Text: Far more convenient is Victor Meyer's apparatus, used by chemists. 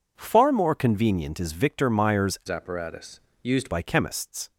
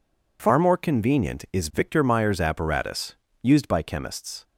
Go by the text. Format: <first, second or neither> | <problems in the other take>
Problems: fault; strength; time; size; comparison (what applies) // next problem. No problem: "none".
second | changes voice from "apparatus" to "used"; from 2.4 to 3.7 s; 1.3 s long